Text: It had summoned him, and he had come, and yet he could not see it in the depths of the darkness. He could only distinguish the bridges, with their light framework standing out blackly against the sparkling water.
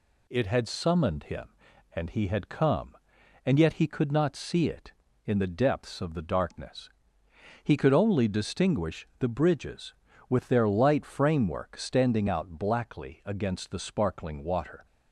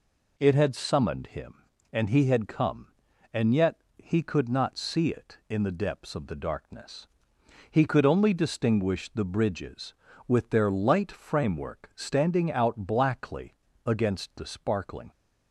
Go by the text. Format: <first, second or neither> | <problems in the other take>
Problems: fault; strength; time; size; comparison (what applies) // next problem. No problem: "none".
first | pauses between "yet" and "he"; slight; at 3.7 s; 0.20 s long // pauses between "blackly" and "against"; slight; at 13.5 s; 0.34 s long // stops before "water"; at 15.1 s